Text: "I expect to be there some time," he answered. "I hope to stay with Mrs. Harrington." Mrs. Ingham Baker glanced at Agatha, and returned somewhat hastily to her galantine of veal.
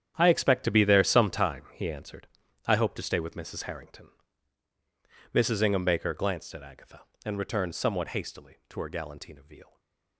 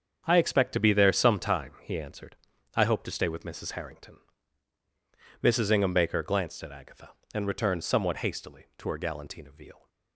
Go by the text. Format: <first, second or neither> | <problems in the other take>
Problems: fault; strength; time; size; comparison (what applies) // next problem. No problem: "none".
second | gets quieter; strong; throughout; 13.5 dB // starts louder than the rest; strong; until 1.1 s; 9.5 dB; strong in the second // stays silent after the last word; slight; from 9.6 s on; 0.5 s long